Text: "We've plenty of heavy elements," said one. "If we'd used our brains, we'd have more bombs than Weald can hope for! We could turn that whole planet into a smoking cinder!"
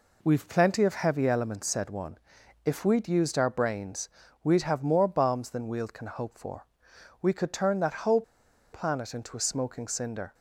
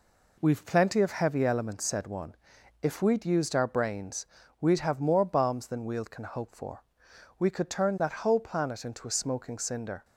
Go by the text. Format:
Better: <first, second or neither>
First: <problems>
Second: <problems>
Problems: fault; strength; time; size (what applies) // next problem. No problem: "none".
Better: second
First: pauses between "whole" and "planet"; noticeable; at 8.2 s; 0.51 s long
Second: none